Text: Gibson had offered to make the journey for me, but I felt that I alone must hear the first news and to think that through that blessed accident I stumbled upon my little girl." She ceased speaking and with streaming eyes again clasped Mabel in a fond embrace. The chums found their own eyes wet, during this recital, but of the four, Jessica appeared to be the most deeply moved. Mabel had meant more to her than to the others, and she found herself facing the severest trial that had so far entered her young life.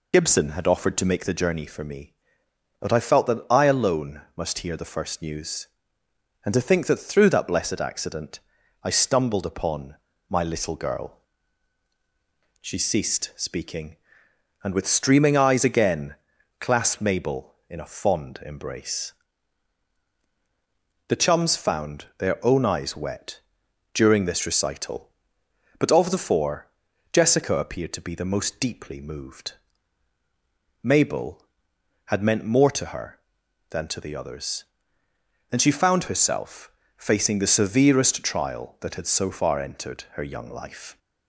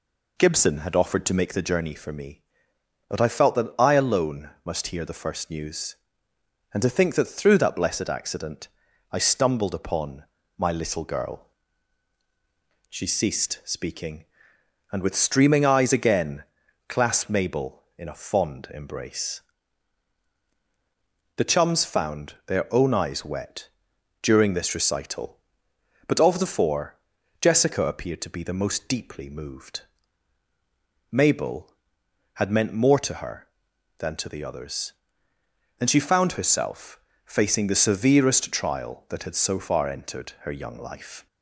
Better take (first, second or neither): second